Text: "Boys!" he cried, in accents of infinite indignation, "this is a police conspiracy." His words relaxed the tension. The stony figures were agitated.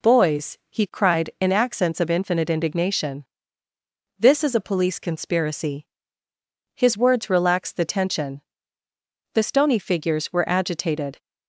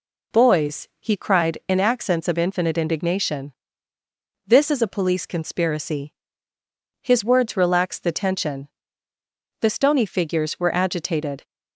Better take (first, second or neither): neither